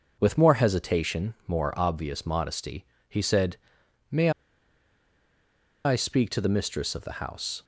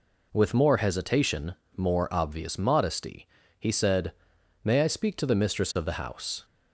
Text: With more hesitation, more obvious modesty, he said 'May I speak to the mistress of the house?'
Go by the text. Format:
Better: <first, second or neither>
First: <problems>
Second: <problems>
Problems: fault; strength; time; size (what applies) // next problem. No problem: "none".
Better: second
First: pauses between "said" and "May"; noticeable; at 3.5 s; 0.56 s long // pauses between "May" and "I"; strong; at 4.2 s; 1.5 s long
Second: pauses between "said" and "May"; noticeable; at 4.1 s; 0.52 s long